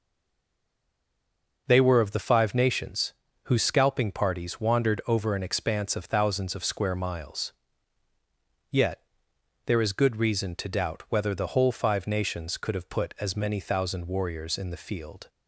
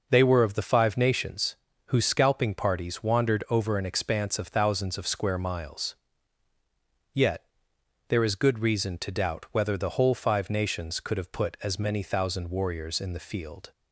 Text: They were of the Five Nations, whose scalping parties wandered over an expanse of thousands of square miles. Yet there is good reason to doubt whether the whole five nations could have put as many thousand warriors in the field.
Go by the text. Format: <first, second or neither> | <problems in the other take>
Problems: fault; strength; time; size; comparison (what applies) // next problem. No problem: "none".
second | stays silent before the first word; noticeable; until 1.6 s; 1.6 s long // pauses between "Yet" and "there"; noticeable; at 9.0 s; 0.66 s long; noticeable in the second